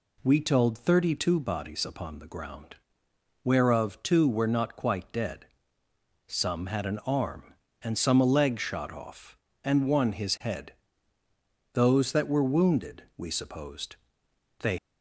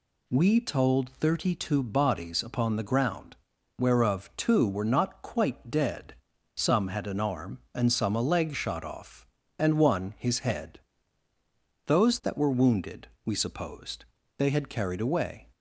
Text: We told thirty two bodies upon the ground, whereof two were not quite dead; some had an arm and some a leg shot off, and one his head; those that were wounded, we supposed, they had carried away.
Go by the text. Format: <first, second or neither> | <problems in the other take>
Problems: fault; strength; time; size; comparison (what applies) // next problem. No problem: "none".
second | stops before "had carried away"; at 14.7 s